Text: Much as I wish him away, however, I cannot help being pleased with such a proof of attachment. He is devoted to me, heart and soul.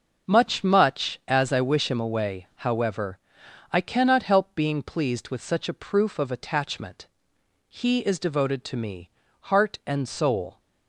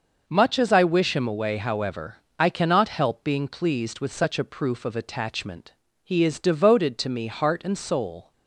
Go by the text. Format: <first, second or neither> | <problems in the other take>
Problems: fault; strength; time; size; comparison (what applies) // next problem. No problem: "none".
second | starts louder than the rest; until 1.3 s; 6 dB // says "Much" twice; at 0.6 s